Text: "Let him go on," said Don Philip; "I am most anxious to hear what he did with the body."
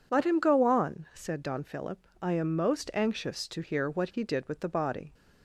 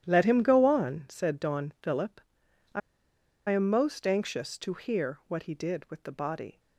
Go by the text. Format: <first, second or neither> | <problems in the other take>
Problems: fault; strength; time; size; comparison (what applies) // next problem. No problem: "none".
first | starts louder than the rest; strong; until 1.0 s; 11 dB // pauses between "I" and "am"; noticeable; at 2.8 s; 0.69 s long